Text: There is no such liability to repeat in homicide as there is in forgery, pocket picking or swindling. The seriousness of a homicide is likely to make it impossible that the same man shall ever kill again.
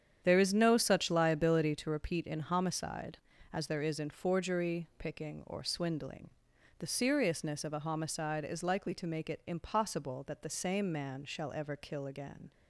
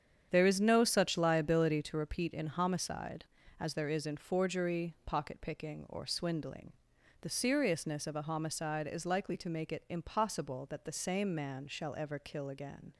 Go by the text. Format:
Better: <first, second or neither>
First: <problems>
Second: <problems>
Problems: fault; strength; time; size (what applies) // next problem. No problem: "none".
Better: second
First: starts louder than the rest; strong; until 1.2 s; 8.5 dB // skips "pocket"; at 4.9 s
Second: starts louder than the rest; strong; until 1.3 s; 8.5 dB